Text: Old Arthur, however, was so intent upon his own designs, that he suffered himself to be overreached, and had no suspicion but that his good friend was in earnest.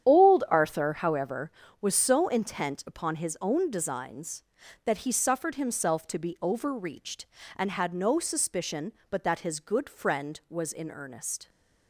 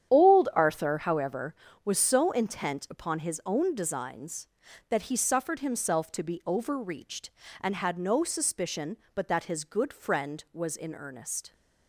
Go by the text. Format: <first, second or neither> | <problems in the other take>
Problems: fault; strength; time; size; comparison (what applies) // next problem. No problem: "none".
neither | starts louder than the rest; strong; the same in both